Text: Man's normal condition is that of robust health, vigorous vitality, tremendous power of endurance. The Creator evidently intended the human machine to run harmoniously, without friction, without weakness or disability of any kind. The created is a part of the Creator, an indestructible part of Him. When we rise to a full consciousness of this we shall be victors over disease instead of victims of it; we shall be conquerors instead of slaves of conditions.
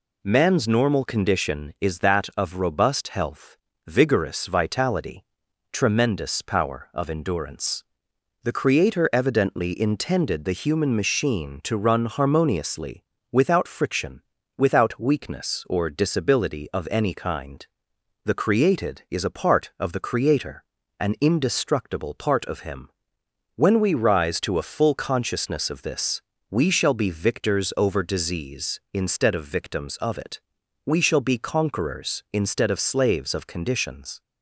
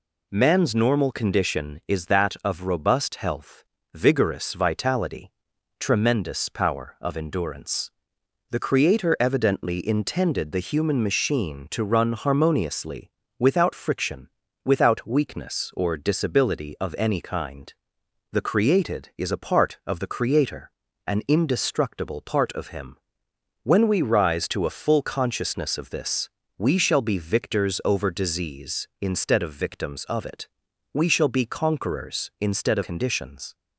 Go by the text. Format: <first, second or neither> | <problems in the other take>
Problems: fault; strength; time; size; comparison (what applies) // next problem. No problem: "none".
first | pauses between "this" and "we"; slight; at 26.3 s; 0.26 s long; slight in the first // skips "slaves of"; at 32.8 s